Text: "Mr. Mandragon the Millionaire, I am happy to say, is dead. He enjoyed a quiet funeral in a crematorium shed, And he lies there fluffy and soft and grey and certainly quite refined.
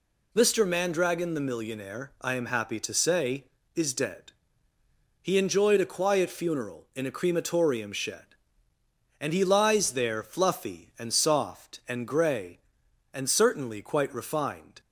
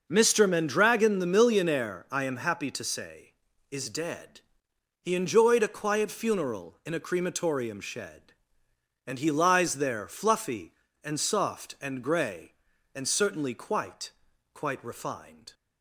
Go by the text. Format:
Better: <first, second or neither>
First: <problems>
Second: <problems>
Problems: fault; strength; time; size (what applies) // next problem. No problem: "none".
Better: first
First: none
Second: says "quite" twice; at 14.5 s